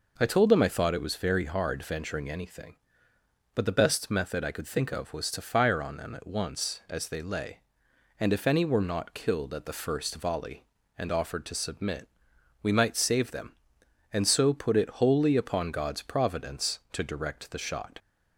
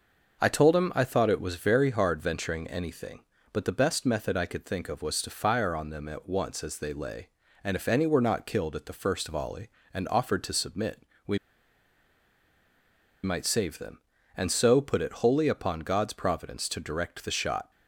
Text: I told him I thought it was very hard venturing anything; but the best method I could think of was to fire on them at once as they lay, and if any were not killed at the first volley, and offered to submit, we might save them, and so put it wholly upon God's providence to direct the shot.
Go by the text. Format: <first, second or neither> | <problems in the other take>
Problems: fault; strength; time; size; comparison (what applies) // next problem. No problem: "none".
first | pauses between "we" and "might"; strong; at 11.3 s; 1.8 s long